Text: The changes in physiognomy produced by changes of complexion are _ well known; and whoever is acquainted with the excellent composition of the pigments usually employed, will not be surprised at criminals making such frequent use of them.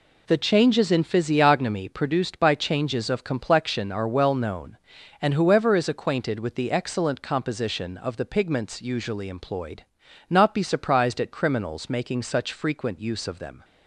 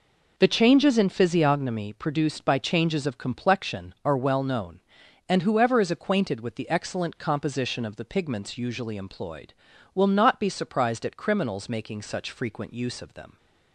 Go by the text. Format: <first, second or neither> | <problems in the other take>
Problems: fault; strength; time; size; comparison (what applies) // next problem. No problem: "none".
second | skips "will"; at 10.0 s